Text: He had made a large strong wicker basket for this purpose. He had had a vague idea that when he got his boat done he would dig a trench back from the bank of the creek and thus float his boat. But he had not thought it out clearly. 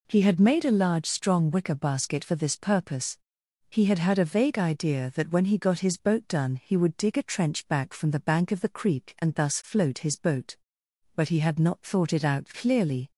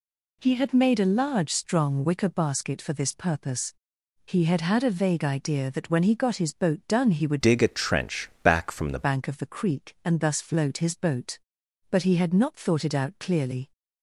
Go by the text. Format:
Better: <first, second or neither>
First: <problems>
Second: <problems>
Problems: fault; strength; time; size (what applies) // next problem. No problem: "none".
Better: first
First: none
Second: changes voice from "dig" to "the"; from 7.4 to 9.0 s; 1.6 s long